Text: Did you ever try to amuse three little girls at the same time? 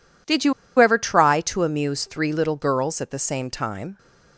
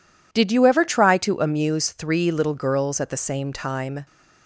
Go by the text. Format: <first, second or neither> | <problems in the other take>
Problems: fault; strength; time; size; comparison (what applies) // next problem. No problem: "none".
second | pauses between "you" and "ever"; slight; at 0.5 s; 0.26 s long